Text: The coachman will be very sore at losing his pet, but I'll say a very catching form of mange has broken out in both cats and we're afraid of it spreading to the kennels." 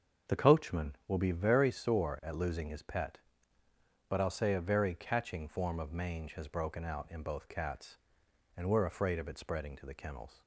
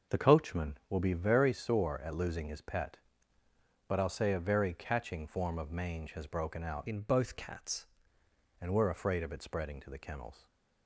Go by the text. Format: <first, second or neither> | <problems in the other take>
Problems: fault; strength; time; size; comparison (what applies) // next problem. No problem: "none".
first | starts louder than the rest; noticeable; until 1.2 s; 6 dB; also in the first // changes voice from "in" to "cats"; from 6.8 to 7.8 s; 1.0 s long // stays silent after the last word; slight; from 10.3 s on; 0.5 s long